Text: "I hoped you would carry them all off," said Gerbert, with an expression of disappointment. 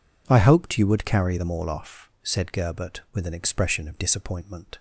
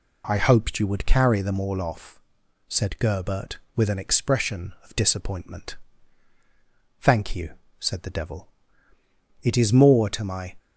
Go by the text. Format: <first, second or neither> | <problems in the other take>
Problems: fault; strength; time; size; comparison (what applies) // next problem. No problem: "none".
first | goes on to say "Thank you said the Devil It is more to my"; strong; from 6.9 s on; 3.5 s long